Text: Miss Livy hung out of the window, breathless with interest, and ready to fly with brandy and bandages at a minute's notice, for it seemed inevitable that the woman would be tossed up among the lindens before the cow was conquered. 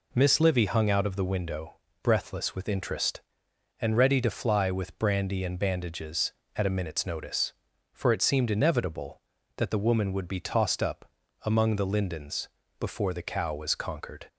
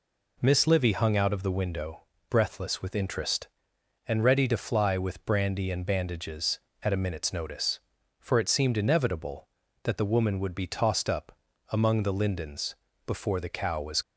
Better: first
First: pauses between "up" and "among"; at 11.0 s; 0.38 s long // pauses between "lindens" and "before"; slight; at 12.4 s; 0.28 s long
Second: pauses between "up" and "among"; at 11.3 s; 0.38 s long // pauses between "lindens" and "before"; slight; at 12.7 s; 0.28 s long // stops before "conquered"; at 14.0 s

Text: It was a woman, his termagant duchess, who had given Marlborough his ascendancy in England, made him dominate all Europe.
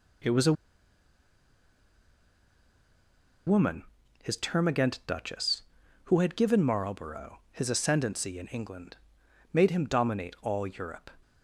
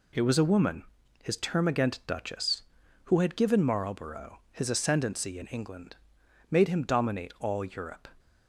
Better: second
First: pauses between "a" and "woman"; strong; at 0.5 s; 2.9 s long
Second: none

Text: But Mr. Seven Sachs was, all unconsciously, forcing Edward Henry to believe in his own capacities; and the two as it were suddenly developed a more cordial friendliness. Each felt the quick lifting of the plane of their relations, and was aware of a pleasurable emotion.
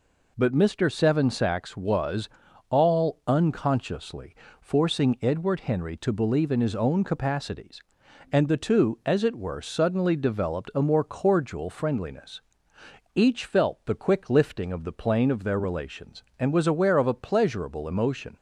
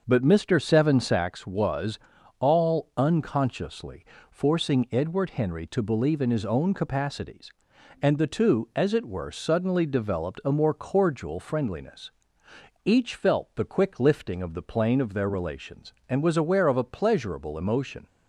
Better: first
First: none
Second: starts louder than the rest; until 1.2 s; 6.5 dB

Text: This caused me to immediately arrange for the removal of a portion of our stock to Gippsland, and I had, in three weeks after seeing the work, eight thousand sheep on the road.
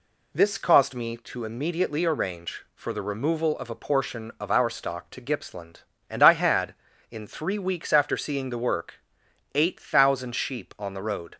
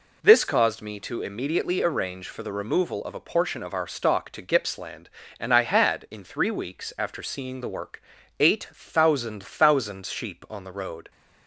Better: first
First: none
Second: says "thousand" twice; at 9.4 s

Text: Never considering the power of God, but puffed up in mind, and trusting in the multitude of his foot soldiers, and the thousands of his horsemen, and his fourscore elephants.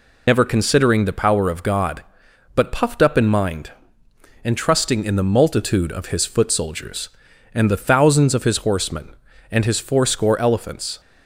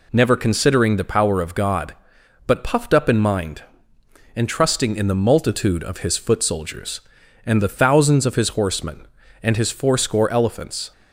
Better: second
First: loses the start of "Never"; at 0.2 s; 95 ms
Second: none

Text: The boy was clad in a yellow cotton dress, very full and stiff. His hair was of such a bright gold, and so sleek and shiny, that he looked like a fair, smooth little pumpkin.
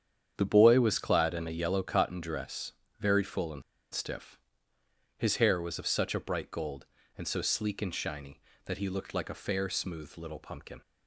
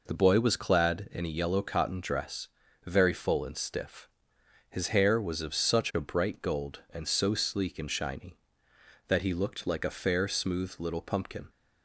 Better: second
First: starts louder than the rest; strong; until 1.3 s; 8.5 dB // pauses between "and" and "stiff"; slight; at 3.6 s; 0.30 s long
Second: none

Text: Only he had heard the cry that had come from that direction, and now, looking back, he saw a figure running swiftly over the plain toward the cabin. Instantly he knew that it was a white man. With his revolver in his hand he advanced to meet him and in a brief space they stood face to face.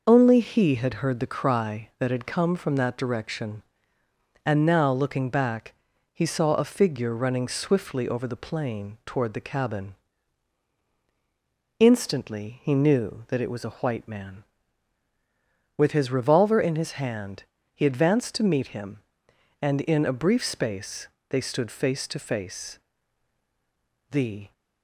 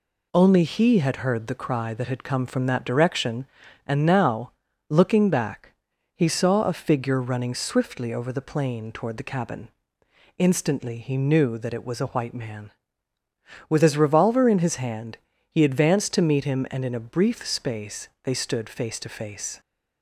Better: second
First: pauses between "hand" and "he"; slight; at 17.4 s; 0.28 s long // pauses between "space" and "they"; slight; at 21.0 s; 0.22 s long // goes on to say "The"; slight; from 24.1 s on; 0.42 s long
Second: pauses between "hand" and "he"; slight; at 15.1 s; 0.32 s long

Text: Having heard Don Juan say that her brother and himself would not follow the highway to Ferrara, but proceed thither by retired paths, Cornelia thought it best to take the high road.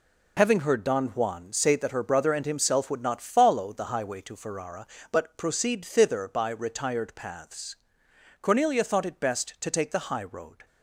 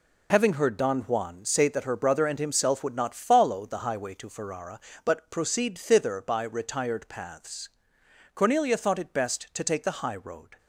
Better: neither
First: none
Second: none

